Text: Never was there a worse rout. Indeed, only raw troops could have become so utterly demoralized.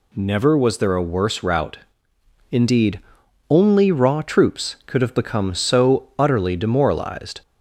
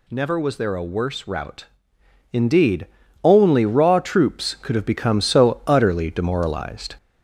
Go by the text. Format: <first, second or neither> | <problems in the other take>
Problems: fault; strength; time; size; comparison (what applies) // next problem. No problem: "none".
first | gets louder; slight; throughout; 2 dB